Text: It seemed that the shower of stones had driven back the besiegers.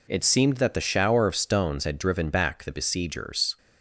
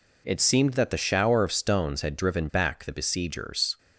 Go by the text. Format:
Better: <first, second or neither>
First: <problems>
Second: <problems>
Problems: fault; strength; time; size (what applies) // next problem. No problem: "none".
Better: neither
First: none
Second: none